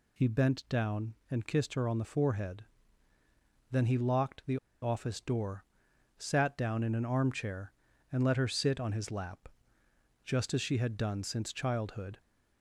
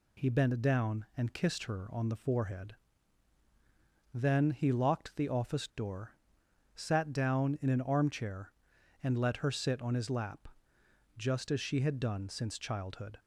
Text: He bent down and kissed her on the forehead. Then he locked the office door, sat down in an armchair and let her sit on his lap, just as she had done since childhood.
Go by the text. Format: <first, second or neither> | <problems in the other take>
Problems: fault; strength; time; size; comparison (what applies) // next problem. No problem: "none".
second | pauses between "the" and "office"; slight; at 4.5 s; 0.25 s long